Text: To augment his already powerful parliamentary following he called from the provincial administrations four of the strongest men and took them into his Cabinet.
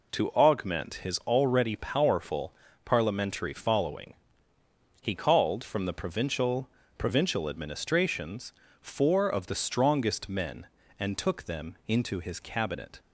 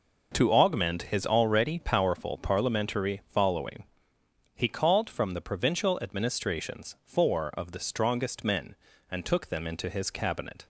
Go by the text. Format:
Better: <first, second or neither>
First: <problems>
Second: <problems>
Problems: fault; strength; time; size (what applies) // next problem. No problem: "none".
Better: second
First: pauses between "powerful" and "parliamentary"; slight; at 2.5 s; 0.32 s long // pauses between "following" and "he"; noticeable; at 4.1 s; 0.88 s long // says "provincial" twice; at 6.9 s // pauses between "administrations" and "four"; slight; at 8.5 s; 0.30 s long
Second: pauses between "following" and "he"; noticeable; at 3.8 s; 0.72 s long